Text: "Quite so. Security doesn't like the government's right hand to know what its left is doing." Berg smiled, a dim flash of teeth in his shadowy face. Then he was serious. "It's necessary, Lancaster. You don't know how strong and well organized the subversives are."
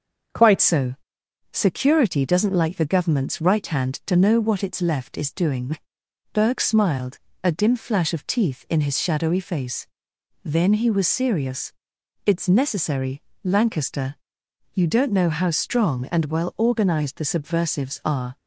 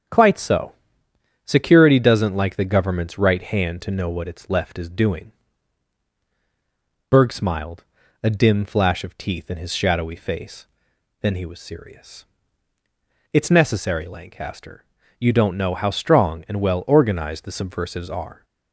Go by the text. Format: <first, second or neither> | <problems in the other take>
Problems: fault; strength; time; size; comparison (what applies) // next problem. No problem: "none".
second | starts louder than the rest; until 1.9 s; 6.5 dB; strong in the second // changes voice at "so"; from 0.6 s on; 17.7 s long